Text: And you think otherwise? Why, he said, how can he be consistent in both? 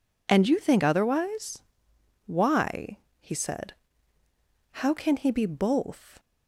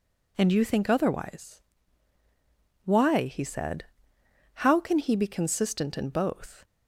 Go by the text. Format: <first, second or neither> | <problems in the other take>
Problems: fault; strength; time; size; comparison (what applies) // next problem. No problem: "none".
second | skips "consistent in"; at 5.4 s